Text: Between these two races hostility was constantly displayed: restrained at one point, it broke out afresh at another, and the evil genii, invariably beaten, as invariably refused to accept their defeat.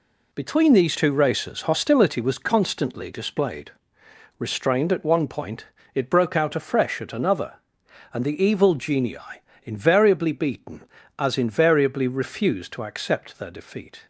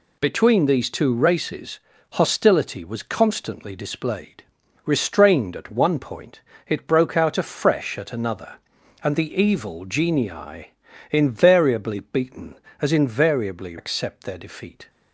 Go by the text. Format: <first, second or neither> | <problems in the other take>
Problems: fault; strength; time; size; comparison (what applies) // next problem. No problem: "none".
first | pauses between "races" and "hostility"; slight; at 1.7 s; 0.36 s long // skips "refused to"; at 13.7 s